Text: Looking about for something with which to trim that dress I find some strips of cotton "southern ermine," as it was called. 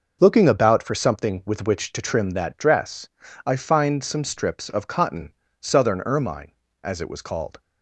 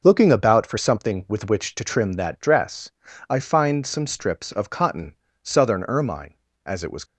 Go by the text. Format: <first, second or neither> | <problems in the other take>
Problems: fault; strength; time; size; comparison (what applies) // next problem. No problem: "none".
first | pauses between "dress" and "I"; at 2.9 s; 0.40 s long; also in the first // pauses between "cotton" and "southern"; slight; at 5.1 s; 0.30 s long; slight in the first // stops before "called"; at 7.0 s